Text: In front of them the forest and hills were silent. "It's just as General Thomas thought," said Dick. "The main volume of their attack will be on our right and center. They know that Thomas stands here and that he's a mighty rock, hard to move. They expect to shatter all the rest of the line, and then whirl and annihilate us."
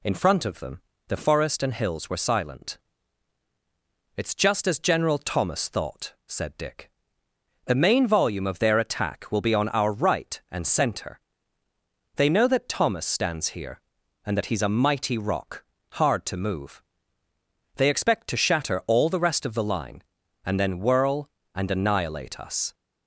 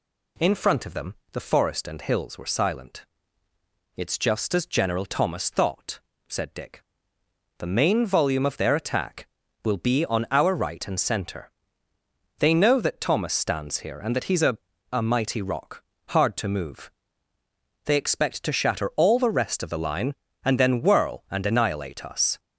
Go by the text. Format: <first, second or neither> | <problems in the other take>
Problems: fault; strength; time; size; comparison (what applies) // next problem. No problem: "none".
first | pauses between "them" and "the"; slight; at 1.1 s; 0.18 s long; slight in the first // says "a" twice; at 14.9 s